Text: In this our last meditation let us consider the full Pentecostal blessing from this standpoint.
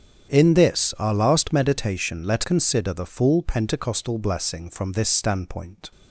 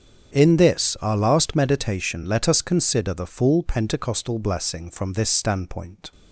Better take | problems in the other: second | starts louder than the rest; strong; until 1.3 s; 8.5 dB; strong in the second // skips "us"; at 2.4 s

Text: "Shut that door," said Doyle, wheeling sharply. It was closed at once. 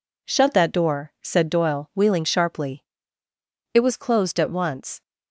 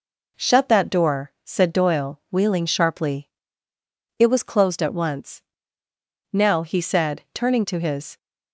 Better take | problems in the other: first | goes on to say "Now he said turning to his"; strong; from 6.3 s on; 1.8 s long

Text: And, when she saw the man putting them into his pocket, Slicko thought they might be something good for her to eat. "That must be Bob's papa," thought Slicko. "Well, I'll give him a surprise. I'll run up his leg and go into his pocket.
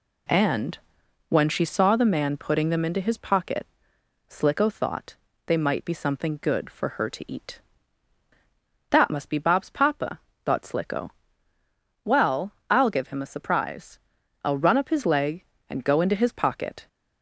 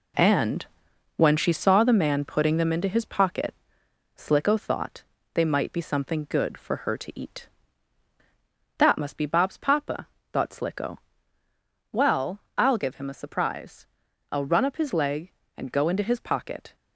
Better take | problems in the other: first | gets quieter; strong; throughout; 7.5 dB // pauses between "thought" and "they"; slight; at 5.0 s; 0.30 s long; slight in the first

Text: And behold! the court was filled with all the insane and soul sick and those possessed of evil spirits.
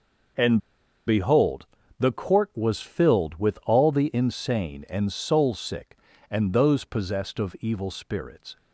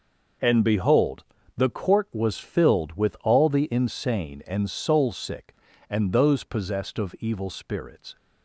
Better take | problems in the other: second | pauses between "And" and "behold"; noticeable; at 0.5 s; 0.47 s long

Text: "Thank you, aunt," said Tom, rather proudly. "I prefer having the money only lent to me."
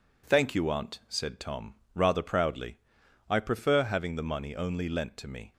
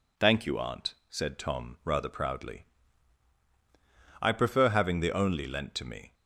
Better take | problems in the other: first | skips "money"; at 5.1 s

